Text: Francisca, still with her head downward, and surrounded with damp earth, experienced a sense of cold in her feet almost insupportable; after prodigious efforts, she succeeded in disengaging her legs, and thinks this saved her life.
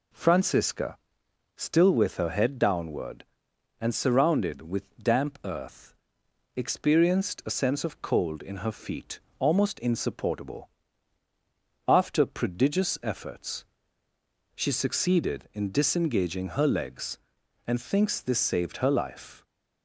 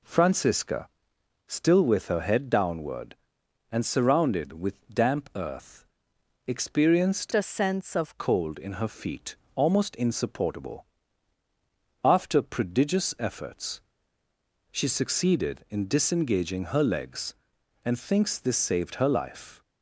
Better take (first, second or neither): first